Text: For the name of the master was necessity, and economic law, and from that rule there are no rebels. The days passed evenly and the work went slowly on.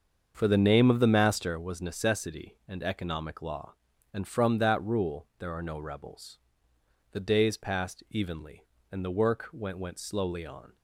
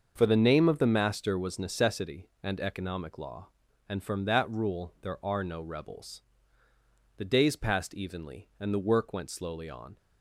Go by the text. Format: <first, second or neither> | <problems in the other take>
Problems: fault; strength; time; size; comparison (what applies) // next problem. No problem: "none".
second | starts louder than the rest; until 1.3 s; 7 dB; also in the second // says "went" twice; at 9.7 s